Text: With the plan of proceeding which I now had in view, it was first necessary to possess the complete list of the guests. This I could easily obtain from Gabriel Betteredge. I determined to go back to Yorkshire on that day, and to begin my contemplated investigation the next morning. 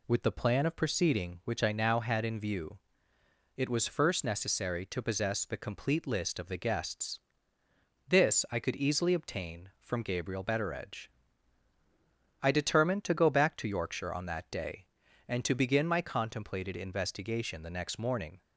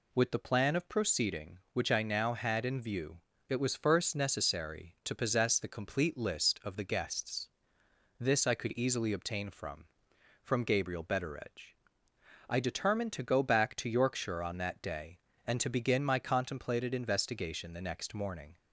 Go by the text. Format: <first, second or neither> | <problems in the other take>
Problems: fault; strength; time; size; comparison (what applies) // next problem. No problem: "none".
first | says "from" twice; at 10.4 s